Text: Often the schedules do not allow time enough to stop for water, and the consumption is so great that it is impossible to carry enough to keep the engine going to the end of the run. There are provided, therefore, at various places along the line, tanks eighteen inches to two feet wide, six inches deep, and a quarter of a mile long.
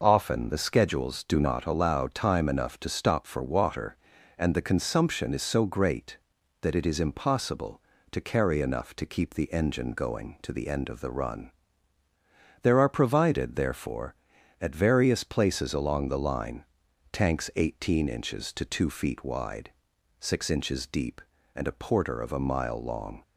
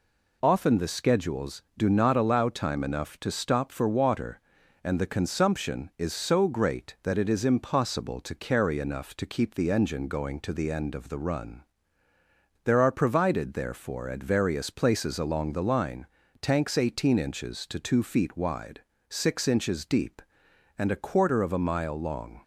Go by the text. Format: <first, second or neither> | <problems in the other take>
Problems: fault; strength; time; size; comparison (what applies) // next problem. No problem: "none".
second | says "porter" for "quarter"; at 21.7 s